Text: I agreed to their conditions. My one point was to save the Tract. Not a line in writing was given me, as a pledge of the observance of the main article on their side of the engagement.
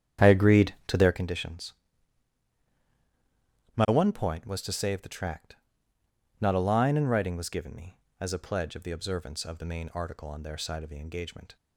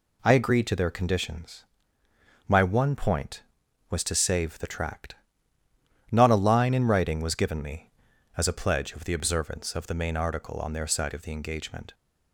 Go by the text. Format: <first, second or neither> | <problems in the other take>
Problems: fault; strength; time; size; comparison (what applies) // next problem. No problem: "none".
second | starts louder than the rest; strong; until 1.2 s; 9.5 dB